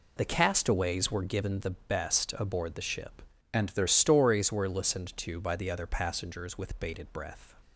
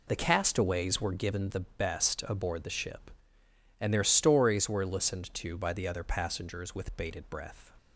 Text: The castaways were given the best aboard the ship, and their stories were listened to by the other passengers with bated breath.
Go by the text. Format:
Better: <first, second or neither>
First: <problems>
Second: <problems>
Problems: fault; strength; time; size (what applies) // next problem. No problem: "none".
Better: second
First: changes voice from "and" to "their"; from 3.5 to 3.8 s; 0.3 s long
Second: none